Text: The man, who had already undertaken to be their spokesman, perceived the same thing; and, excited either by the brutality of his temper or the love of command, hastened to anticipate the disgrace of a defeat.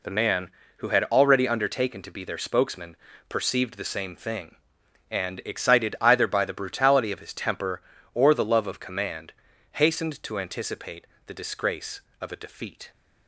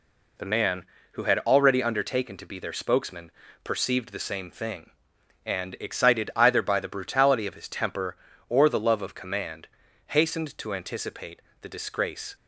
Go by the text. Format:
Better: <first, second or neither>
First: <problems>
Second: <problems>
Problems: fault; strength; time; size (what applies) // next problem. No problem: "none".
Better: first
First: pauses between "anticipate" and "the"; slight; at 11.0 s; 0.20 s long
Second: pauses between "anticipate" and "the"; slight; at 11.4 s; 0.20 s long // stops before "of a defeat"; at 12.3 s